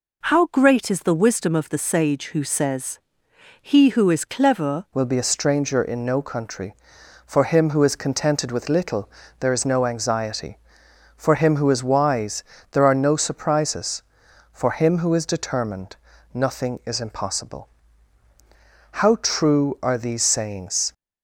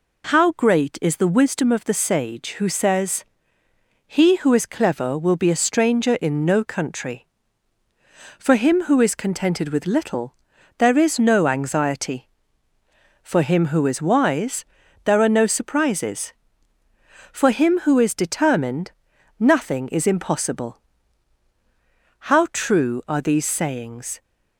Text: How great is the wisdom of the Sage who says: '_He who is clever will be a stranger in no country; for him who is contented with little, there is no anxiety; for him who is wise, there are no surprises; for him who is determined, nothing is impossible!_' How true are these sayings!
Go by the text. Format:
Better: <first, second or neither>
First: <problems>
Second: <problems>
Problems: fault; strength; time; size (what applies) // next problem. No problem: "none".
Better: second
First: changes voice at "will"; from 4.9 s on; 16.0 s long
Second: none